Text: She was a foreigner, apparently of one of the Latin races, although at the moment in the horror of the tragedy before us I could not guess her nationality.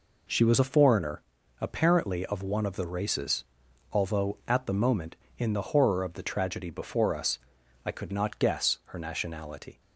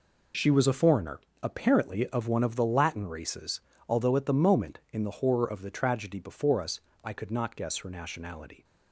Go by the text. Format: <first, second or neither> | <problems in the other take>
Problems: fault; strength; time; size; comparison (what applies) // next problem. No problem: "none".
second | skips "Latin"; at 2.8 s // pauses between "us" and "I"; noticeable; at 7.3 s; 0.48 s long; slight in the second